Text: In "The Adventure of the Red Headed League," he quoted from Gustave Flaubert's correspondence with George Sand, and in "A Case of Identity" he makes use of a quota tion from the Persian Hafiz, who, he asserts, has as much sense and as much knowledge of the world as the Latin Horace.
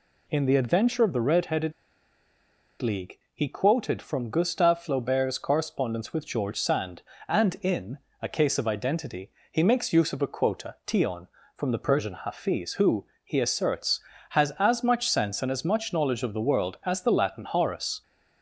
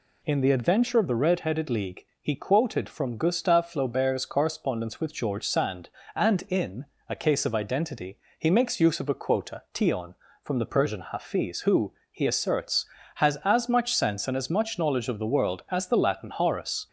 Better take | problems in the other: second | pauses between "Headed" and "League"; at 1.7 s; 1.0 s long // pauses between "in" and "A"; slight; at 7.9 s; 0.24 s long; slight in the second // pauses between "Identity" and "he"; slight; at 9.3 s; 0.18 s long; slight in the second

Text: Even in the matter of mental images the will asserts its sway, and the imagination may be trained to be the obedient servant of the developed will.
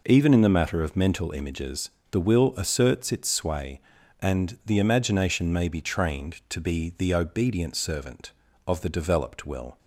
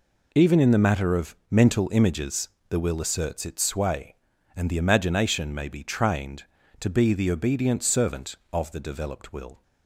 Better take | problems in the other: neither | pauses between "images" and "the"; slight; the same in both

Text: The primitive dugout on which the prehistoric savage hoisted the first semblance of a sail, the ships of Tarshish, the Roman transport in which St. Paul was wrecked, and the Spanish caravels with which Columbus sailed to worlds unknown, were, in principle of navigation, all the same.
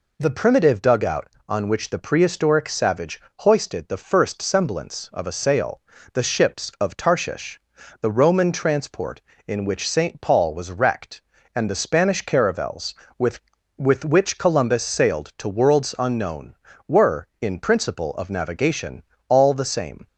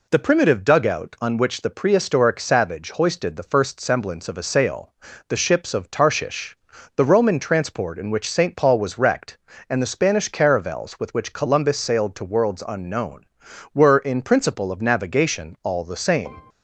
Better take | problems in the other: second | pauses between "savage" and "hoisted"; slight; at 3.2 s; 0.18 s long // says "with" twice; at 13.7 s

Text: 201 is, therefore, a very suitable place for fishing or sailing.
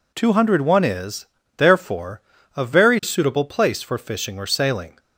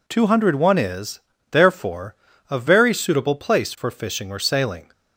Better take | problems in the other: neither | none

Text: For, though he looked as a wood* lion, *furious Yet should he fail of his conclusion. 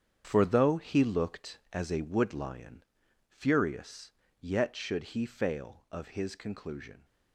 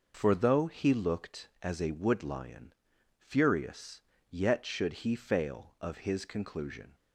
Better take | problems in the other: second | gets quieter; strong; throughout; 10 dB // pauses between "furious" and "Yet"; slight; at 4.0 s; 0.30 s long; slight in the second

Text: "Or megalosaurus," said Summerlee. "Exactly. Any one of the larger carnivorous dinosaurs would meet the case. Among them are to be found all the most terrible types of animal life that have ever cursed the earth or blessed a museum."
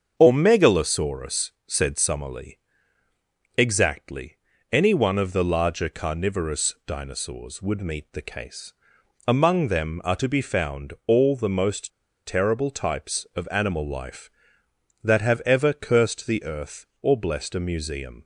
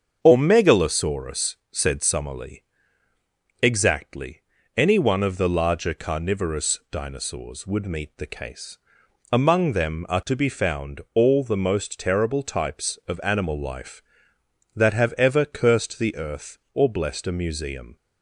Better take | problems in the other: second | starts louder than the rest; until 1.1 s; 7 dB; also in the second // pauses between "most" and "terrible"; slight; at 11.8 s; 0.35 s long

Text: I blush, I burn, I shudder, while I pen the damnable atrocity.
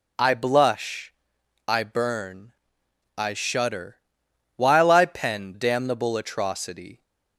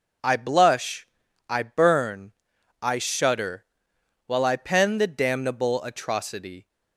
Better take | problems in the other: second | skips "the"; at 5.5 s

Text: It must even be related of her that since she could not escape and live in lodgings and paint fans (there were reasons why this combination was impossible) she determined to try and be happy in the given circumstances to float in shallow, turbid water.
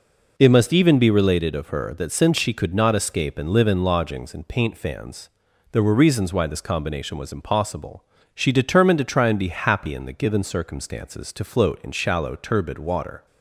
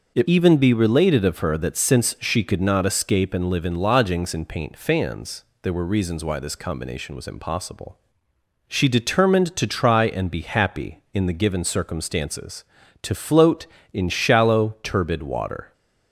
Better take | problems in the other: first | starts louder than the rest; noticeable; until 1.1 s; 6 dB // skips "must"; at 0.2 s

